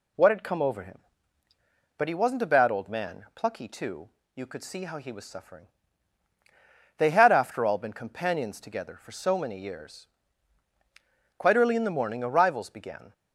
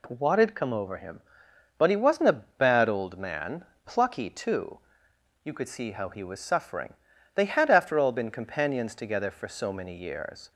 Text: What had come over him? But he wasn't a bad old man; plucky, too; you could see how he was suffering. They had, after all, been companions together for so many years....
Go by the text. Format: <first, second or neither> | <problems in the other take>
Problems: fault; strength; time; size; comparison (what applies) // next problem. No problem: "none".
second | goes on to say "Quite early in the morning arrivals began"; strong; from 11.3 s on; 1.7 s long